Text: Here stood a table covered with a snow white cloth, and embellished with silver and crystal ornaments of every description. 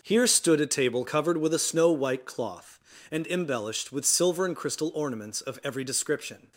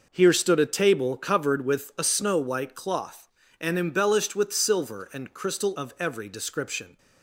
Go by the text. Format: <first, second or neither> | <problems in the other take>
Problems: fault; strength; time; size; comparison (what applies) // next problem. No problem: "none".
first | skips "ornaments"; at 5.7 s